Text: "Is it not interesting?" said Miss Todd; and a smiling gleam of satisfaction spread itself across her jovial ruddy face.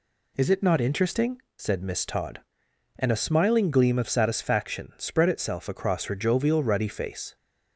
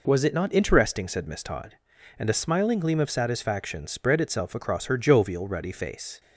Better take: first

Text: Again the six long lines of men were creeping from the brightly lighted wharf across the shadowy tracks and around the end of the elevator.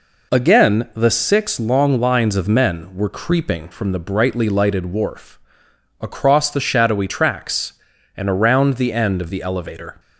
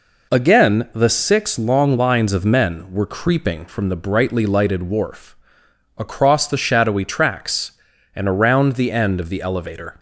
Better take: neither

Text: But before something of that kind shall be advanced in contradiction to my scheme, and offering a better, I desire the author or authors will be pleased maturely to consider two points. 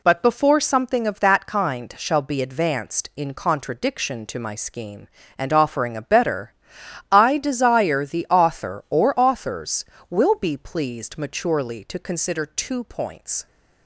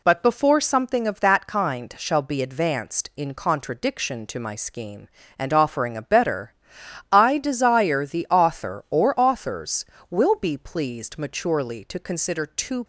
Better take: first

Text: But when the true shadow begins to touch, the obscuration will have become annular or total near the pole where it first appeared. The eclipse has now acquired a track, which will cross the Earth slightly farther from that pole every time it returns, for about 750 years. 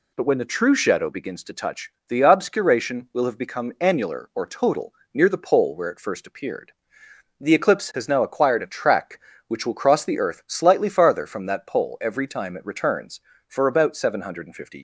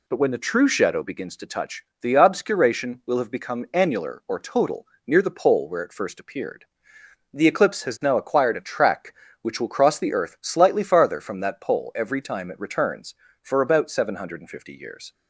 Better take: second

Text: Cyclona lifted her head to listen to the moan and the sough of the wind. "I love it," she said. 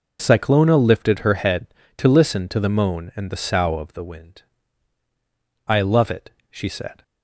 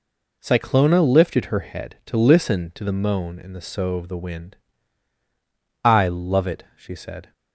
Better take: neither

